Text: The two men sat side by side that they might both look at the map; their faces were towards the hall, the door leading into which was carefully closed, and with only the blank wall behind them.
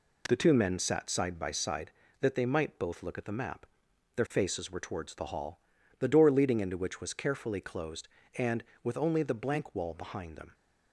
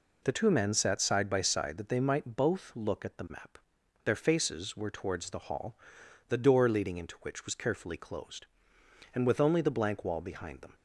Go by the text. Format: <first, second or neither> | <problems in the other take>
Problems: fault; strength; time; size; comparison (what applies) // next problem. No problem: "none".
neither | none